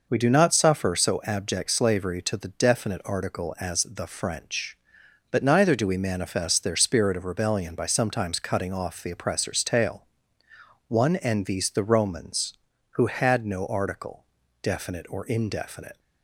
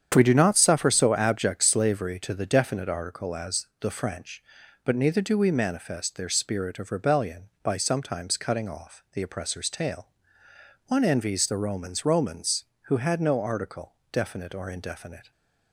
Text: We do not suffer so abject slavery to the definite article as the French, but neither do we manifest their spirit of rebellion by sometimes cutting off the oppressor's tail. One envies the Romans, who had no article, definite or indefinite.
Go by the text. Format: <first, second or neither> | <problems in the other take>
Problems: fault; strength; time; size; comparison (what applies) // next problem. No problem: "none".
first | starts louder than the rest; strong; until 1.1 s; 8.5 dB // says "Romans" twice; at 12.0 s